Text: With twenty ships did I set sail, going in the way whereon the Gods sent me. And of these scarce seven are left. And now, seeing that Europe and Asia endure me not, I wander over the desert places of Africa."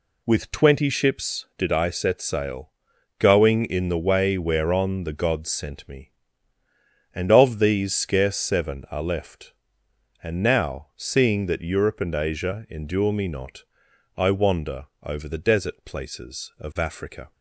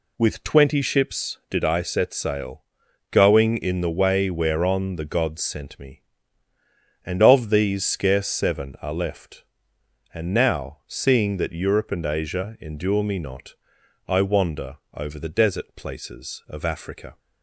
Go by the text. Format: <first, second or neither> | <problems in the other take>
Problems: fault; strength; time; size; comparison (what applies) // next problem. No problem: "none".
neither | none